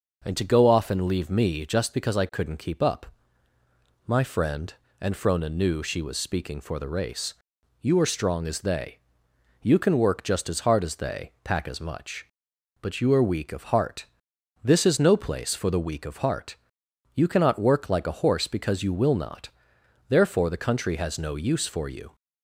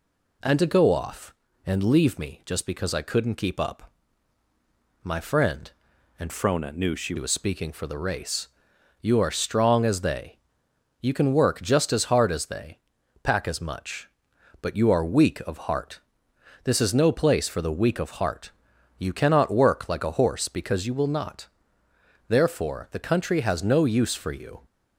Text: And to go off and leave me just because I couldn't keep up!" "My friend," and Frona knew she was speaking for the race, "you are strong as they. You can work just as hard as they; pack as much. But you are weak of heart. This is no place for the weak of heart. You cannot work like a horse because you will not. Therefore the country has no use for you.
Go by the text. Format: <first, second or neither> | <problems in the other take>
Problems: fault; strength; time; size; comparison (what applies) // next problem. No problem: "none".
first | changes voice from "Frona" to "she"; from 6.2 to 7.1 s; 0.9 s long